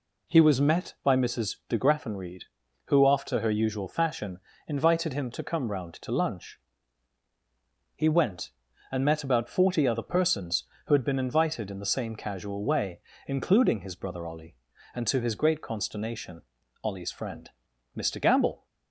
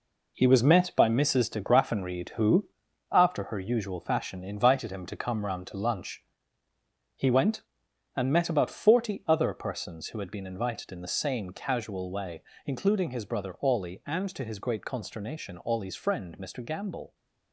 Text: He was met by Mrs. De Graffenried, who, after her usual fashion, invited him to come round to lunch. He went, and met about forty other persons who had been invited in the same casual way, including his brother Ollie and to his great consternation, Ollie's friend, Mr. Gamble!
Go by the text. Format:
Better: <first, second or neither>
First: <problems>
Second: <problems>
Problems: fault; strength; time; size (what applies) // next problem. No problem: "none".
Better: first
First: none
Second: gets quieter; strong; throughout; 8 dB